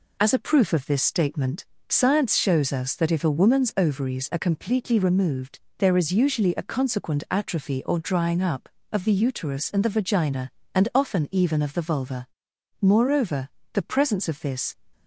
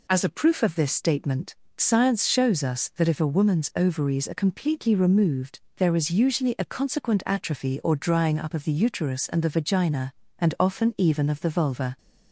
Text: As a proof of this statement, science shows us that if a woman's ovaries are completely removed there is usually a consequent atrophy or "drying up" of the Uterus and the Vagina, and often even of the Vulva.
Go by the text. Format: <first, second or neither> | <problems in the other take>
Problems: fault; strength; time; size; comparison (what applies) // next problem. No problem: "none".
second | pauses between "removed" and "there"; slight; at 5.5 s; 0.20 s long; slight in the second // goes on to say "Moreover the presence of this"; strong; from 12.8 s on; 1.9 s long